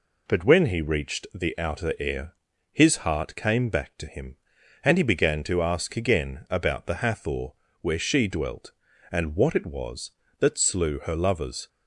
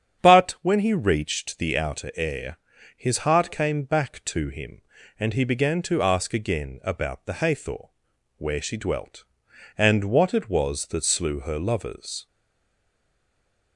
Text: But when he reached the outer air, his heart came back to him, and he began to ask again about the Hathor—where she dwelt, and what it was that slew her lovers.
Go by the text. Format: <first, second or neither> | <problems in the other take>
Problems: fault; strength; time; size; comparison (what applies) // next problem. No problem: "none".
first | starts louder than the rest; strong; until 1.2 s; 8 dB // stays silent after the last word; noticeable; from 12.2 s on; 1.5 s long